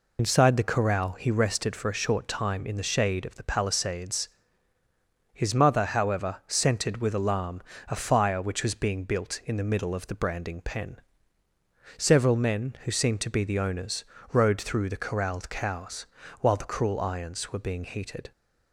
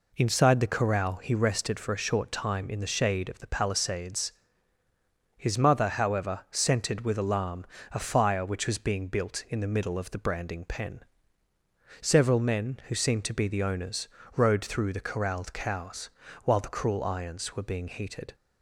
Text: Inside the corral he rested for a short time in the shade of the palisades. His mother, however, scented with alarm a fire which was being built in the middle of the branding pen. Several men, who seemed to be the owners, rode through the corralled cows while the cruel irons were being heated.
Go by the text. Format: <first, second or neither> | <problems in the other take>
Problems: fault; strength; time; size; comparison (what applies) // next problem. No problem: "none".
second | loses the start of "Inside"; at 0.1 s; 85 ms // pauses between "alarm" and "a"; slight; at 7.6 s; 0.28 s long; slight in the second // pauses between "cows" and "while"; slight; at 16.0 s; 0.34 s long; slight in the second